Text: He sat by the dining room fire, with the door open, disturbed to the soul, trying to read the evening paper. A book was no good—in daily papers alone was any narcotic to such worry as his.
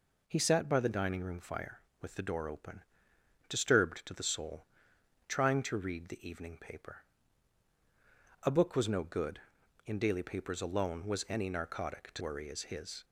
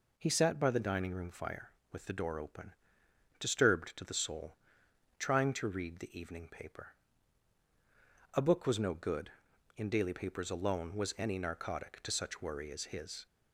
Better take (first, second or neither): second